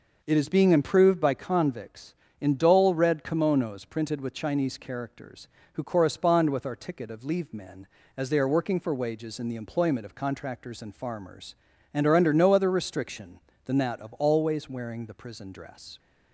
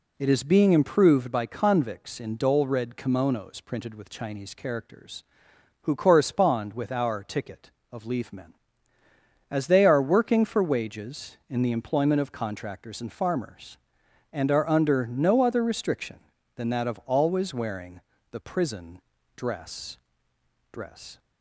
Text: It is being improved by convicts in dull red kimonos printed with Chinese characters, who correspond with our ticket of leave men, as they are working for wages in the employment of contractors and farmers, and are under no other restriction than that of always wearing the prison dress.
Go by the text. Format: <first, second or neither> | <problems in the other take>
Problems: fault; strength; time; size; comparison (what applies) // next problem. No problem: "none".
first | pauses between "wearing" and "the"; slight; at 18.0 s; 0.30 s long // pauses between "prison" and "dress"; slight; at 19.0 s; 0.34 s long // says "dress" twice; at 20.7 s